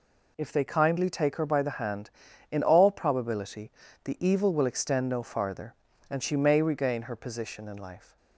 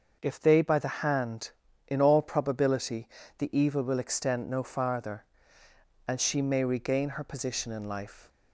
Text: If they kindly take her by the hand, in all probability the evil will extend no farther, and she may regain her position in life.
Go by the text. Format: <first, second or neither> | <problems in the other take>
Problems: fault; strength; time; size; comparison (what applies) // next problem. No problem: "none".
first | starts louder than the rest; until 1.2 s; 6.5 dB // skips "kindly take her"; at 0.6 s // pauses between "probability" and "the"; slight; at 3.0 s; 0.30 s long; slight in the first